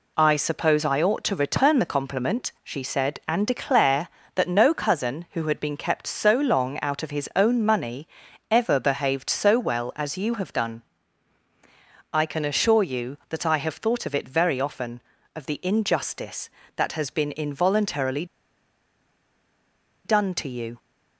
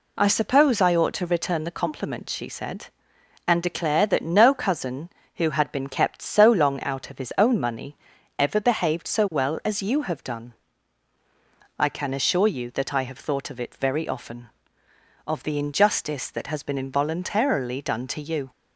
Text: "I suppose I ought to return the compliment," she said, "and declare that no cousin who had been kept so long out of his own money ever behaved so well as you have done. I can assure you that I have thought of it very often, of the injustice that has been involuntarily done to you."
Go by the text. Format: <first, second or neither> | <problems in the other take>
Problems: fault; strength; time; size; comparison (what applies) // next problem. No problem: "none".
second | pauses between "money" and "ever"; at 8.0 s; 0.44 s long; also in the second // pauses between "involuntarily" and "done"; strong; at 18.2 s; 1.8 s long